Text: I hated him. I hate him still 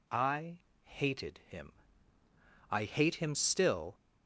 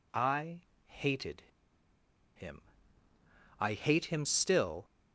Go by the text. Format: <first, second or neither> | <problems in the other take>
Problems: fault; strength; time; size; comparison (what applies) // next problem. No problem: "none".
first | pauses between "I" and "hated"; slight; at 0.6 s; 0.26 s long; slight in the first // pauses between "hated" and "him"; noticeable; at 1.4 s; 0.93 s long